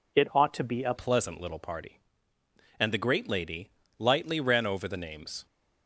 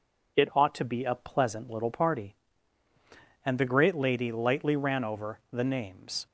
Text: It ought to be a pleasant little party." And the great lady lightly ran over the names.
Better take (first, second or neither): second